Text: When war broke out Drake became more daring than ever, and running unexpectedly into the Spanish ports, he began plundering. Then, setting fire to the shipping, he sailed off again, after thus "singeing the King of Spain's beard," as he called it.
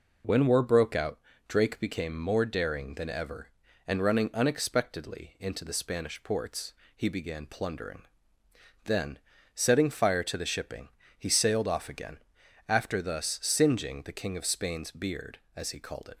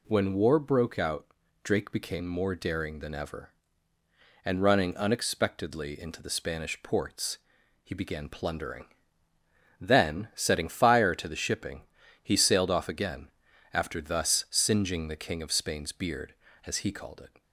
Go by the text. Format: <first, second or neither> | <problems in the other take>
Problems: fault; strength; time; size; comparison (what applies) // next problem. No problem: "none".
neither | pauses between "out" and "Drake"; the same in both